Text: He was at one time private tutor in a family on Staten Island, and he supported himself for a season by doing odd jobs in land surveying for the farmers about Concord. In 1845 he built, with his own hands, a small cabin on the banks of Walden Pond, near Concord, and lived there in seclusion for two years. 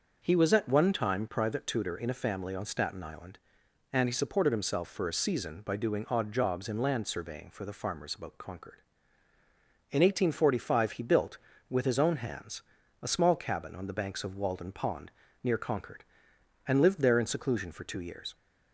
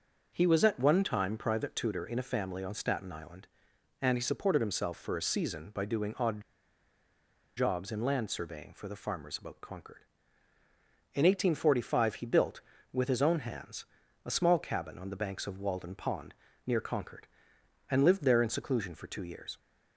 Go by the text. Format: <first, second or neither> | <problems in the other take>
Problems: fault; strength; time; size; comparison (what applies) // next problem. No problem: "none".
first | starts louder than the rest; until 1.3 s; 6 dB; also in the first // pauses between "odd" and "jobs"; at 6.4 s; 1.1 s long